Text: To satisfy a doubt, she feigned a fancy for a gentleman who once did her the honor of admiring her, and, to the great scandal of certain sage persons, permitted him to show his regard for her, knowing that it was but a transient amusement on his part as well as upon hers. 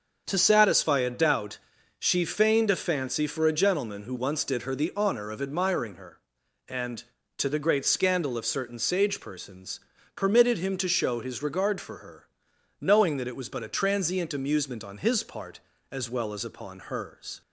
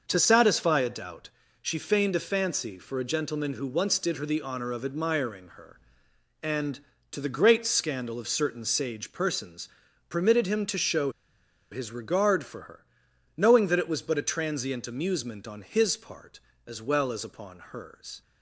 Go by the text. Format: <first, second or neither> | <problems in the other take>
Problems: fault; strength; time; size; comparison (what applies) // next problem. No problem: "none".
first | starts louder than the rest; noticeable; until 1.0 s; 6 dB; also in the first // pauses between "show" and "his"; noticeable; at 11.0 s; 0.61 s long